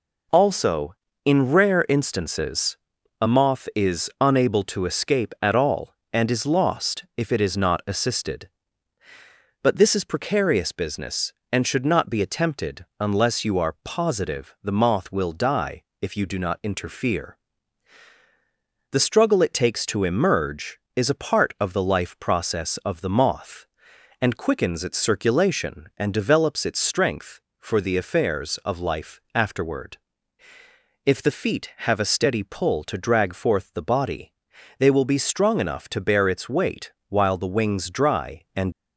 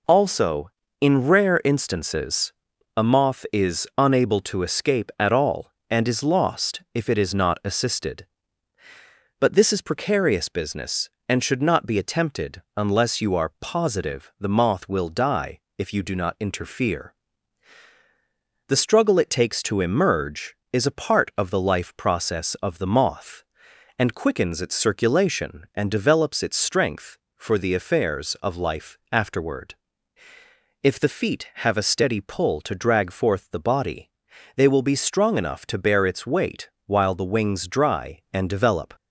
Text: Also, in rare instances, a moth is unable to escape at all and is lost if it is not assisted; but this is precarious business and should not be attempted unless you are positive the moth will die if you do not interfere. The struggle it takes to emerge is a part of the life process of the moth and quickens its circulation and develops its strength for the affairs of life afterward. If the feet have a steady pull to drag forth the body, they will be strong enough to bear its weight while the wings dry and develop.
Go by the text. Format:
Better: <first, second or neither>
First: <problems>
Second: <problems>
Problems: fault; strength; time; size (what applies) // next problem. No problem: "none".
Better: second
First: pauses between "attempted" and "unless"; slight; at 12.8 s; 0.16 s long // pauses between "die" and "if"; slight; at 15.8 s; 0.18 s long // pauses between "weight" and "while"; slight; at 36.9 s; 0.18 s long // stops before "develop"; at 38.7 s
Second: pauses between "attempted" and "unless"; slight; at 12.5 s; 0.16 s long // pauses between "die" and "if"; slight; at 15.5 s; 0.18 s long // pauses between "weight" and "while"; slight; at 36.6 s; 0.18 s long